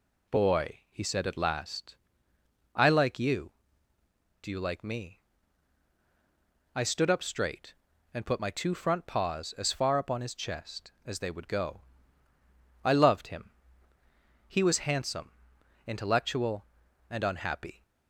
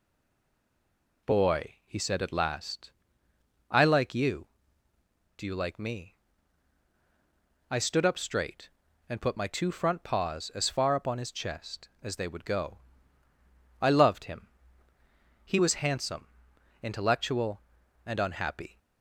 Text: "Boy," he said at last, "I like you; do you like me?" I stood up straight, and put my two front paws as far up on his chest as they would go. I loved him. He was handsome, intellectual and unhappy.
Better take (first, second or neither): first